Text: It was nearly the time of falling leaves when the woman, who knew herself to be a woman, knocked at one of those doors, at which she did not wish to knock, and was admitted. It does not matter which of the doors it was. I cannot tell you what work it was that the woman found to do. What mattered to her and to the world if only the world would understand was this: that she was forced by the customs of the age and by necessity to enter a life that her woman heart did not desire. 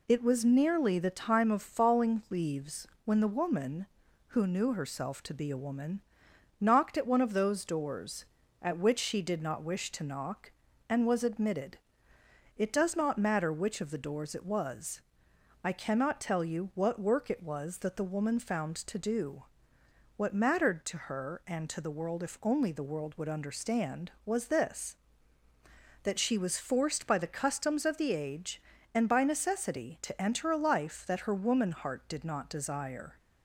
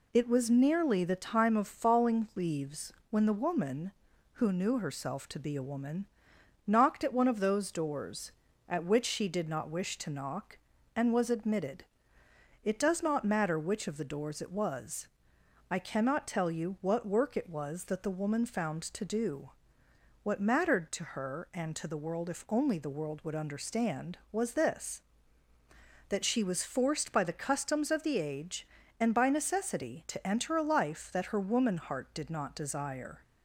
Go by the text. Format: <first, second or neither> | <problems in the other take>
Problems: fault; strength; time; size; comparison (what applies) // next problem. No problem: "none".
neither | pauses between "leaves" and "when"; slight; the same in both